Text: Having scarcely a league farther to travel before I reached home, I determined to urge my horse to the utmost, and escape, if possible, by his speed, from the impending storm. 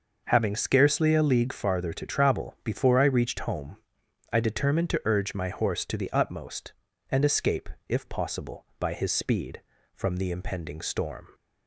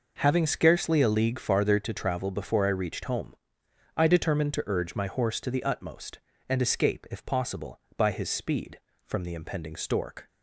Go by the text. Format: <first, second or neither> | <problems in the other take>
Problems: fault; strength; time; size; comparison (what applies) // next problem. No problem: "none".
first | says "stork" for "storm"; at 9.7 s